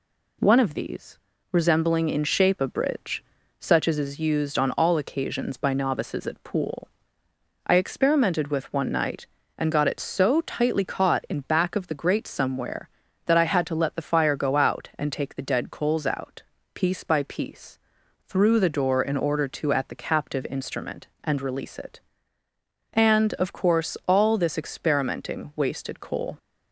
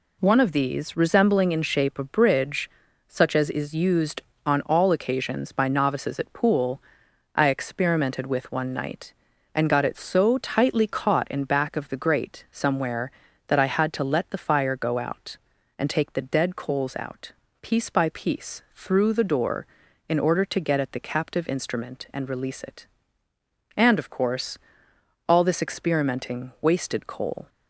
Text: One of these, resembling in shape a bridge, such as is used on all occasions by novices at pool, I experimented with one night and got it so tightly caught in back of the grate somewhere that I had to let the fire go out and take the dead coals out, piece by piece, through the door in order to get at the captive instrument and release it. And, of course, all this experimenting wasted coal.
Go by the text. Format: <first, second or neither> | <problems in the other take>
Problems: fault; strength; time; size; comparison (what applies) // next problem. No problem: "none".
second | skips "get"; at 19.7 s